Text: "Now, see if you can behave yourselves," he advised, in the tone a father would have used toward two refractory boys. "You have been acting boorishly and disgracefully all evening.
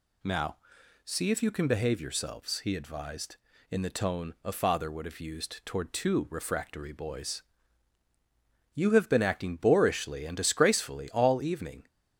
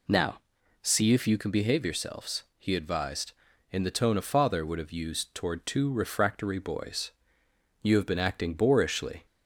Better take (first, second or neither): first